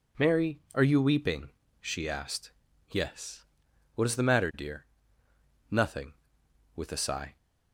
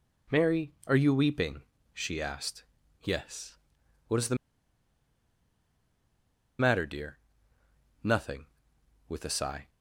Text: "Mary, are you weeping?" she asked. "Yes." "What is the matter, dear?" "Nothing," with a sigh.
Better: first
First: none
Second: pauses between "the" and "matter"; strong; at 4.3 s; 2.2 s long

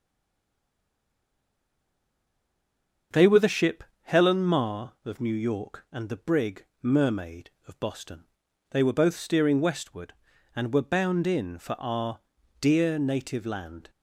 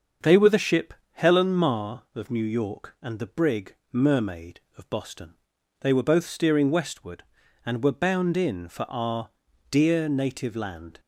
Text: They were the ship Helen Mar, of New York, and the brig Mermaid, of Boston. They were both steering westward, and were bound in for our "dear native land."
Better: second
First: stays silent before the first word; strong; until 3.1 s; 3.1 s long // starts louder than the rest; until 4.3 s; 7 dB // pauses between "ship" and "Helen"; slight; at 3.8 s; 0.20 s long // pauses between "brig" and "Mermaid"; slight; at 6.6 s; 0.18 s long // pauses between "our" and "dear"; at 12.1 s; 0.42 s long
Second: starts louder than the rest; until 1.4 s; 7 dB // pauses between "ship" and "Helen"; slight; at 0.9 s; 0.20 s long // pauses between "brig" and "Mermaid"; slight; at 3.7 s; 0.18 s long // pauses between "our" and "dear"; at 9.2 s; 0.42 s long

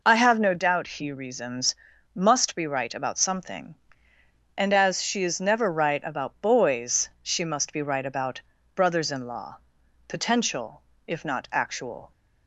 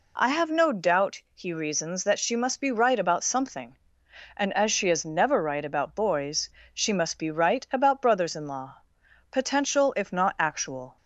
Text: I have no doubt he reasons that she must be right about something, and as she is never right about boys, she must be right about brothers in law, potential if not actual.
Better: second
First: skips "that she"; at 1.9 s // pauses between "about" and "brothers"; slight; at 8.4 s; 0.32 s long // pauses between "potential" and "if"; slight; at 10.8 s; 0.24 s long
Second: none

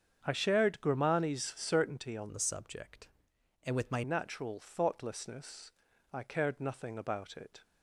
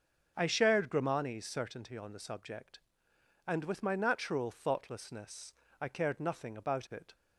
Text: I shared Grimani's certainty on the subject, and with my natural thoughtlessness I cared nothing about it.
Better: second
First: starts louder than the rest; strong; until 1.2 s; 7.5 dB // changes voice from "the" to "my"; from 2.3 to 4.0 s; 1.7 s long // pauses between "thoughtlessness" and "I"; at 5.6 s; 0.42 s long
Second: starts louder than the rest; until 1.3 s; 6 dB // pauses between "thoughtlessness" and "I"; slight; at 5.5 s; 0.28 s long

